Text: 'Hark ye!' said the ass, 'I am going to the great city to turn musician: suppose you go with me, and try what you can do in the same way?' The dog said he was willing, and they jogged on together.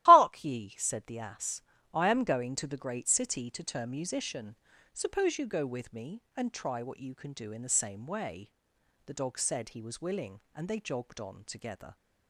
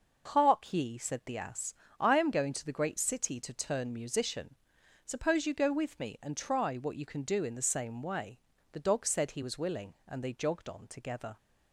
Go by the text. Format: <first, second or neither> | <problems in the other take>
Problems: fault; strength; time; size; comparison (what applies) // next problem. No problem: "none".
second | loses the start of "Hark"; at 0.0 s; 40 ms // starts louder than the rest; strong; until 1.0 s; 15 dB